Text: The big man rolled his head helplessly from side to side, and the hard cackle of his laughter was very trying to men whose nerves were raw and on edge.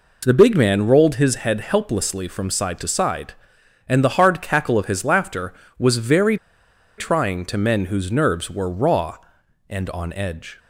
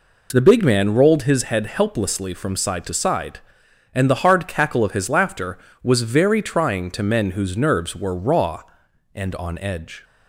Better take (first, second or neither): second